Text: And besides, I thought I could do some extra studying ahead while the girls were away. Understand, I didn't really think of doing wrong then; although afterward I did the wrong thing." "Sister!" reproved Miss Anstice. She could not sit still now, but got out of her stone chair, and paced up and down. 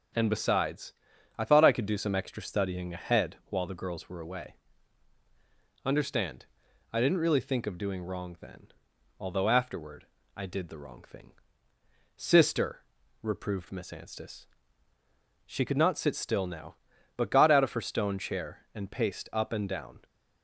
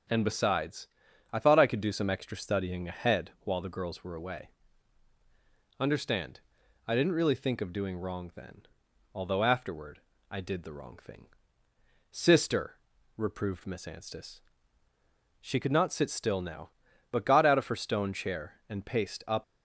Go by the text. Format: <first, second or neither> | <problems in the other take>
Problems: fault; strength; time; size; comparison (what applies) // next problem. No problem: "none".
first | starts louder than the rest; until 1.5 s; 7 dB; also in the first // pauses between "afterward" and "I"; slight; at 10.0 s; 0.30 s long; slight in the first // stops before "and down"; at 19.4 s